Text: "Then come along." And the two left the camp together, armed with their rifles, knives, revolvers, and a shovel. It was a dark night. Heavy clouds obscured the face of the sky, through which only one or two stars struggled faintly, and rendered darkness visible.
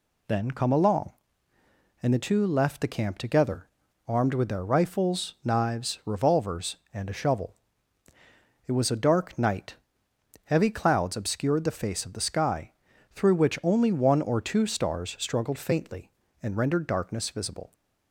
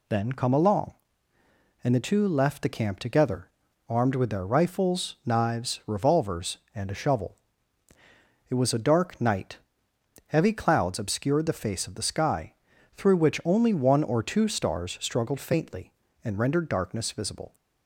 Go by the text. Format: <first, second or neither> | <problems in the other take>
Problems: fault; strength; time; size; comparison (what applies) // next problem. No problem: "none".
neither | none